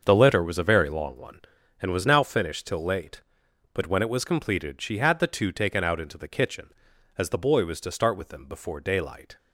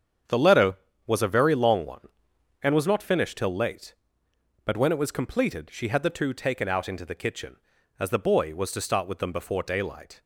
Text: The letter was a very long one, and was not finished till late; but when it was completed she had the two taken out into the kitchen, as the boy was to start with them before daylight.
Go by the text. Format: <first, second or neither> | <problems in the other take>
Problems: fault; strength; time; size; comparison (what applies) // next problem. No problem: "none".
second | starts louder than the rest; until 1.0 s; 7 dB; strong in the second // says "now" for "not"; at 2.0 s